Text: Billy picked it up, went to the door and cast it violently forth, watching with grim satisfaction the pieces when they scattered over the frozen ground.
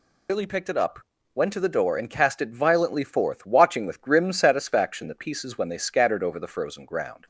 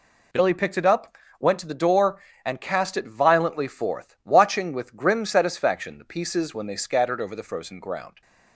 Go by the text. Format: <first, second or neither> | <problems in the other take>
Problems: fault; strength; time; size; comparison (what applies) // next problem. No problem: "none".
second | loses the start of "Billy"; at 0.2 s; 40 ms